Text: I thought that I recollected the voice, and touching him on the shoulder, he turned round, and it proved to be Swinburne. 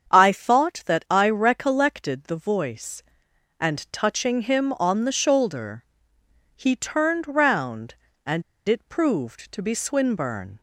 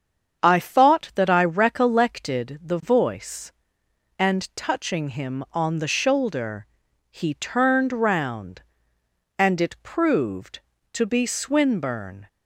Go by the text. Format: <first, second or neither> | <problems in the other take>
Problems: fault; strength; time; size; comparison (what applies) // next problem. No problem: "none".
second | starts louder than the rest; strong; until 1.1 s; 7.5 dB; strong in the second // pauses between "and" and "it"; slight; at 8.4 s; 0.26 s long